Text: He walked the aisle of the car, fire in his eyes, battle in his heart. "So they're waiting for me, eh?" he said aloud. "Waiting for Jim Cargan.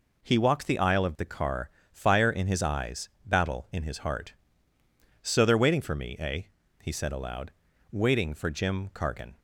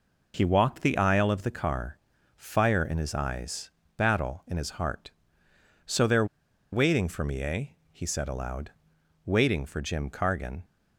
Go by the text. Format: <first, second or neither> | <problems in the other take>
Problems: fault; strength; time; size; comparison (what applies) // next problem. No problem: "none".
first | pauses between "they're" and "waiting"; noticeable; at 6.2 s; 0.47 s long